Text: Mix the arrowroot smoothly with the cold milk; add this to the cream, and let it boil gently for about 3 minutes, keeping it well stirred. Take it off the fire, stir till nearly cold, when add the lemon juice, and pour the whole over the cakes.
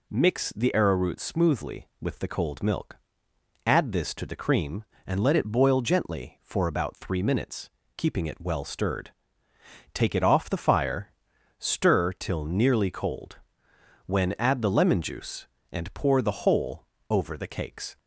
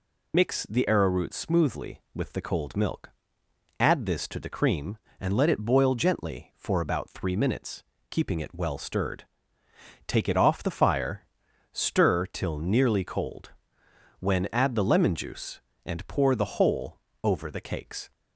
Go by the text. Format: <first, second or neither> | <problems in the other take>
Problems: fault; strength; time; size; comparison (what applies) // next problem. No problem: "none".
first | loses the start of "Mix"; at 0.3 s; 115 ms // pauses between "whole" and "over"; slight; at 16.9 s; 0.24 s long; slight in the first